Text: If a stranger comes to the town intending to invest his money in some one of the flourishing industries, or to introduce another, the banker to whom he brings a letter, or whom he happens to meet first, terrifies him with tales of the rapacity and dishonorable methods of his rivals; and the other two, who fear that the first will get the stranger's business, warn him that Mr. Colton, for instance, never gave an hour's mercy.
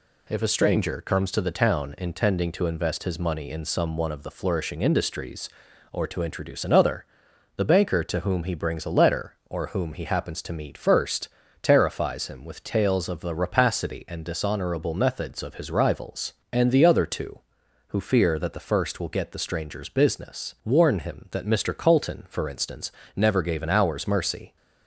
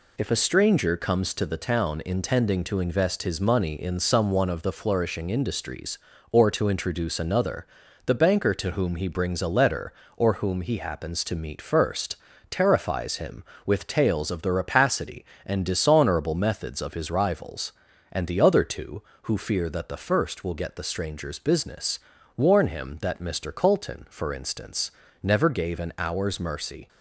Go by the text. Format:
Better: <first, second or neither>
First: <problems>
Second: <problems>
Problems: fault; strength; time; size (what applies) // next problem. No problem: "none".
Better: neither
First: none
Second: none